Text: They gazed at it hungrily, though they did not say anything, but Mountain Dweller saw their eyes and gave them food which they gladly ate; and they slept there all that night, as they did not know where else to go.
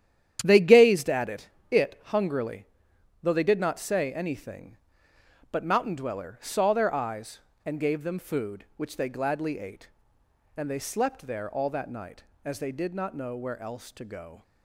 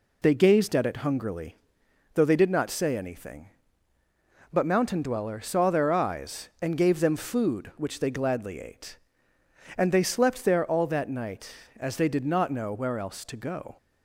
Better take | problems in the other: second | starts louder than the rest; strong; until 1.4 s; 10 dB // says "it" twice; at 1.7 s

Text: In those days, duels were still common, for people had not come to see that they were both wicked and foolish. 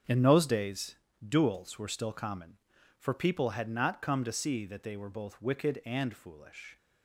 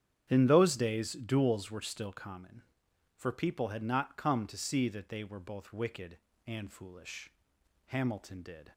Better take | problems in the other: first | starts louder than the rest; strong; until 1.3 s; 9 dB; strong in the first // goes on to say "Hamilton did"; noticeable; from 7.8 s on; 0.86 s long

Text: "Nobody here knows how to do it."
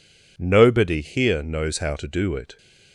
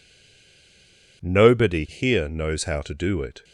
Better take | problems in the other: first | stays silent before the first word; noticeable; until 1.2 s; 1.2 s long

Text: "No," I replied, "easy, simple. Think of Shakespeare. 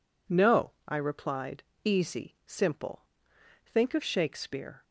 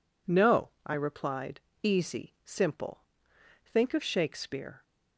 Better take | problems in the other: neither | none

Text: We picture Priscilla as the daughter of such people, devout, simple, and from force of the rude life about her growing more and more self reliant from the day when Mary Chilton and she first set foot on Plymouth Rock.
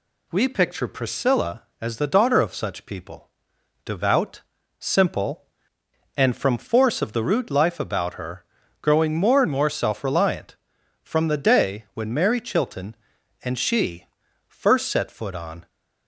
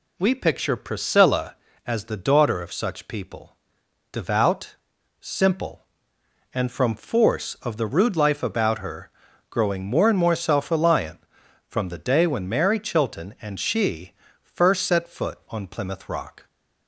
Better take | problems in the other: second | pauses between "her" and "growing"; at 8.4 s; 0.38 s long; also in the second // pauses between "she" and "first"; at 14.0 s; 0.44 s long; slight in the second // stops before "Plymouth Rock"; at 15.6 s

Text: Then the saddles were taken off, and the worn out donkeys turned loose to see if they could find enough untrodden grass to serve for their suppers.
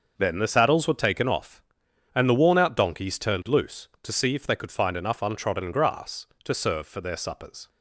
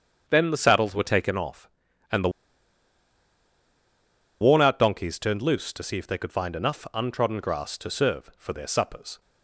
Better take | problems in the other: first | starts louder than the rest; strong; until 1.2 s; 7.5 dB; noticeable in the first // pauses between "the" and "worn"; strong; at 2.2 s; 2.1 s long

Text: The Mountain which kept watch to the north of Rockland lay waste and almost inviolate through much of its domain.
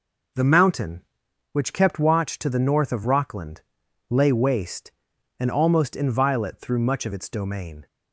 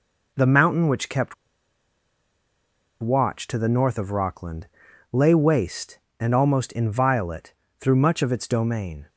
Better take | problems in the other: first | pauses between "kept" and "watch"; strong; at 1.3 s; 1.6 s long // pauses between "Rockland" and "lay"; at 4.6 s; 0.42 s long; noticeable in the first // pauses between "inviolate" and "through"; slight; at 7.5 s; 0.28 s long

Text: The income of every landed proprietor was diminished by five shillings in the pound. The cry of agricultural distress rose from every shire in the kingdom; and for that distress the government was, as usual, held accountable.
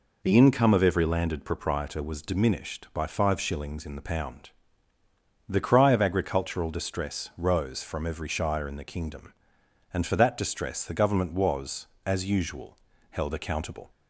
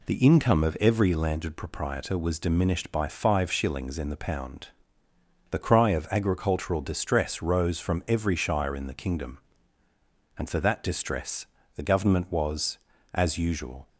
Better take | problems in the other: first | pauses between "distress" and "the"; slight; at 11.4 s; 0.30 s long // stops before "held accountable"; at 13.8 s

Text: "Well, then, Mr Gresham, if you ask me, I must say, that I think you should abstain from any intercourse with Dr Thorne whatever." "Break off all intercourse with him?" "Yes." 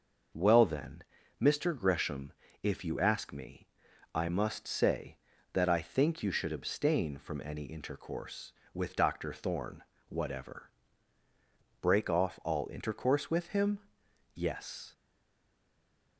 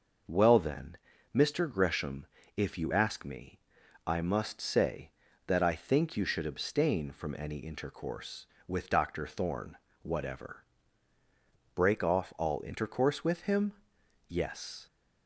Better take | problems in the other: second | starts louder than the rest; noticeable; until 1.7 s; 6 dB; noticeable in the second // pauses between "Thorne" and "whatever"; slight; at 9.8 s; 0.26 s long; slight in the second // stays silent after the last word; noticeable; from 14.9 s on; 1.2 s long

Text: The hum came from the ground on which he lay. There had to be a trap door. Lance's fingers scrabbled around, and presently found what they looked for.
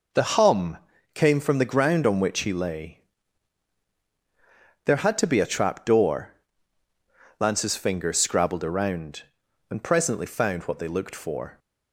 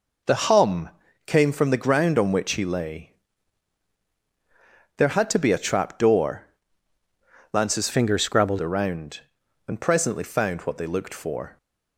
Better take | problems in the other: first | pauses between "hum" and "came"; at 0.8 s; 0.38 s long; also in the first // changes voice from "fingers" to "scrabbled"; from 7.9 to 8.5 s; 0.6 s long

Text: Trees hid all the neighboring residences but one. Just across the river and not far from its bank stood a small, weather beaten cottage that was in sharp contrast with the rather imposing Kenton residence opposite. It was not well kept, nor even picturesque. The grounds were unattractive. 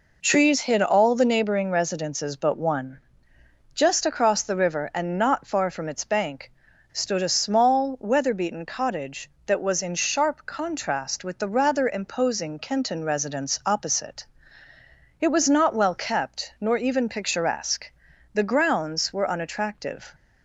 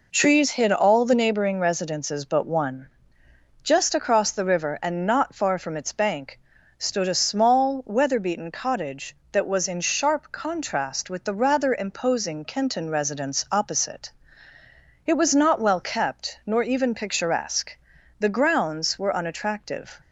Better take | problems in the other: neither | pauses between "bank" and "stood"; the same in both

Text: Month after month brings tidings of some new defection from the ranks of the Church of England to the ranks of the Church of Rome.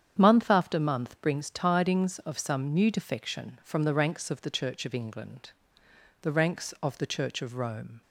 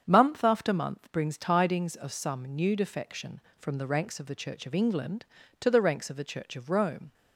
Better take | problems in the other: second | starts louder than the rest; strong; until 1.2 s; 8.5 dB; strong in the second // skips "to"; at 5.8 s

